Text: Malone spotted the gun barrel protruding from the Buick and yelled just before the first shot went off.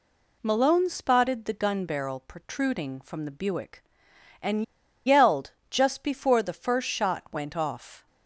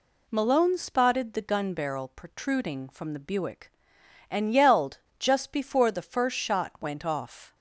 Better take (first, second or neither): second